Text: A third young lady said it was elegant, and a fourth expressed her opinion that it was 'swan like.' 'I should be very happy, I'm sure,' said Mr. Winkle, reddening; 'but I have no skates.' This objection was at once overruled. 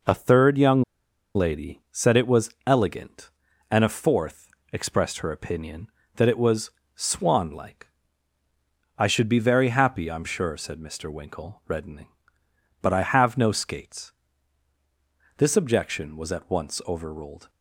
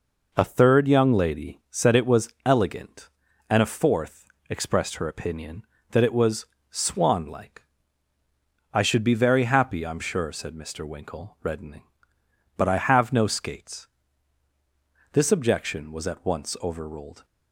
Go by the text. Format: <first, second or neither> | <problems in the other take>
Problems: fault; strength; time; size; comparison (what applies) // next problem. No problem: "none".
second | pauses between "young" and "lady"; noticeable; at 0.8 s; 0.52 s long // pauses between "fourth" and "expressed"; slight; at 4.5 s; 0.20 s long; slight in the second // pauses between "was" and "swan"; slight; at 6.6 s; 0.24 s long; slight in the second